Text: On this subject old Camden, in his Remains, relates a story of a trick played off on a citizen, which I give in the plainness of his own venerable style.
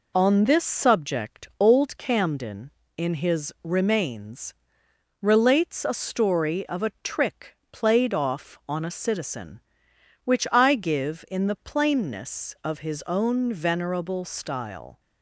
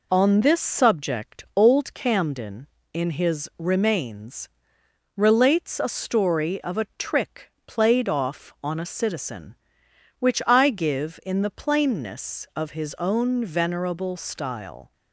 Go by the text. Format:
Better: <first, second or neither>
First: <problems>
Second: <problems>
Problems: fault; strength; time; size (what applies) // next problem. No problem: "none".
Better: neither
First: pauses between "trick" and "played"; slight; at 7.5 s; 0.16 s long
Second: pauses between "trick" and "played"; slight; at 7.4 s; 0.16 s long